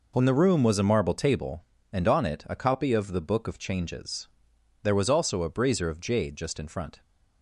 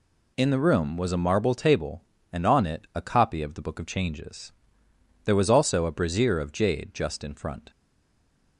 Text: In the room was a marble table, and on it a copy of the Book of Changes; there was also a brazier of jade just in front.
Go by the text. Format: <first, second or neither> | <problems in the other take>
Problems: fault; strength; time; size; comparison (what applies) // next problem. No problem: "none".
first | stays silent after the last word; slight; from 7.7 s on; 0.8 s long